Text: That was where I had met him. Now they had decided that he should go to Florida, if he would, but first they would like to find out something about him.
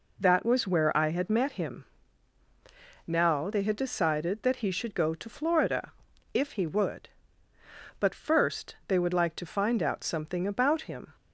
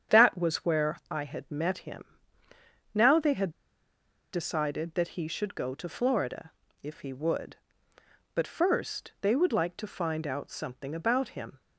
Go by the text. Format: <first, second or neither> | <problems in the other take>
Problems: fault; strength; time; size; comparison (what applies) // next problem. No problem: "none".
first | starts louder than the rest; strong; until 1.2 s; 8 dB // pauses between "had" and "decided"; noticeable; at 3.4 s; 0.83 s long